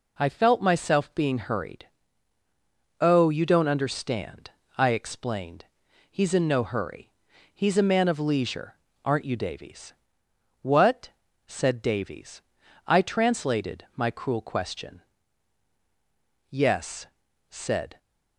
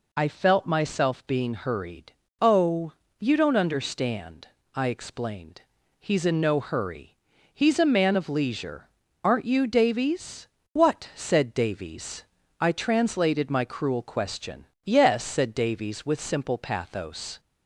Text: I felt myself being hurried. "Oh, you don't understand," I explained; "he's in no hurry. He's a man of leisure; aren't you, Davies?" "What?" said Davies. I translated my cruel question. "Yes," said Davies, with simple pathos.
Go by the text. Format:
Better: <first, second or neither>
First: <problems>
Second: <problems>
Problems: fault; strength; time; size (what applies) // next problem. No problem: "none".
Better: second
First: stops before "Davies with simple pathos"; at 17.9 s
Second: none